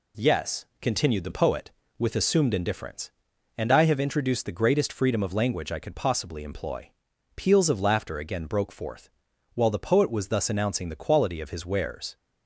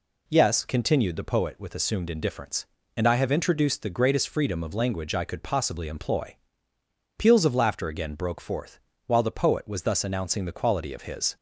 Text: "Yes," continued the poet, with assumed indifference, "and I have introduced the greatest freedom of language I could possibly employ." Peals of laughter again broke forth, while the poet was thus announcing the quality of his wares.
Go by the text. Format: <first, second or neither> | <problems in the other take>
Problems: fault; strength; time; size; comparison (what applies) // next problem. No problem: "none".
first | stops before "wares"; at 11.3 s